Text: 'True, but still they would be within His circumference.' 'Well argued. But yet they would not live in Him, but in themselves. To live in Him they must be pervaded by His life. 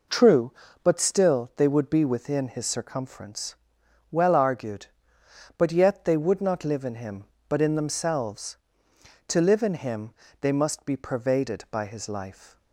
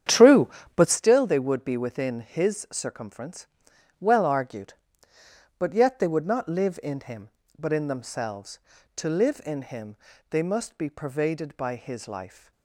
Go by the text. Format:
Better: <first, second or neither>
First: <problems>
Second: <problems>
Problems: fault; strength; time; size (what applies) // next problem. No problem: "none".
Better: first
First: pauses between "Him" and "they"; slight; at 10.1 s; 0.28 s long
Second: starts louder than the rest; strong; until 1.0 s; 9 dB // pauses between "Him" and "they"; slight; at 9.9 s; 0.34 s long